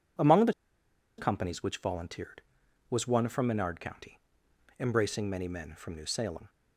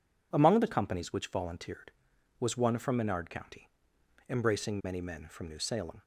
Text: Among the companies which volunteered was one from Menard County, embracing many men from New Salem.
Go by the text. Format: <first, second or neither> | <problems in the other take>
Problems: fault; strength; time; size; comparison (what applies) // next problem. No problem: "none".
second | pauses between "the" and "companies"; noticeable; at 0.5 s; 0.65 s long